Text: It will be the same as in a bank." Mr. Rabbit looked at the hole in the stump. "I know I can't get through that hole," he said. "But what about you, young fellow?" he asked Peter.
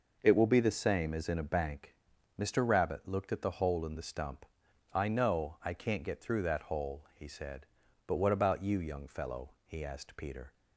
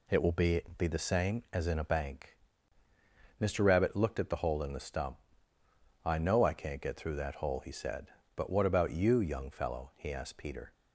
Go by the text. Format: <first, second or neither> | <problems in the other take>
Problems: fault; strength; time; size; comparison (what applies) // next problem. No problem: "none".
first | says "be" twice; at 0.7 s